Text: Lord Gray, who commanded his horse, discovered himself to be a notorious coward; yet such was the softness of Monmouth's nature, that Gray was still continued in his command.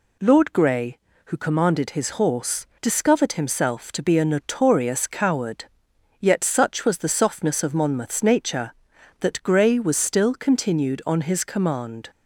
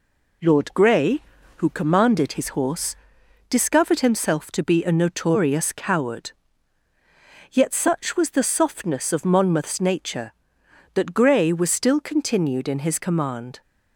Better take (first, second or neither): second